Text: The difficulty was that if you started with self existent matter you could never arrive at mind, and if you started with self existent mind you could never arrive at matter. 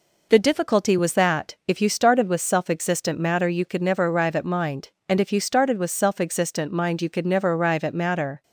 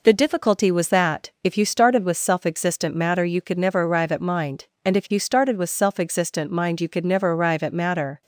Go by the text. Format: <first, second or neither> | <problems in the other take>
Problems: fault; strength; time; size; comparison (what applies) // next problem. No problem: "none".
neither | none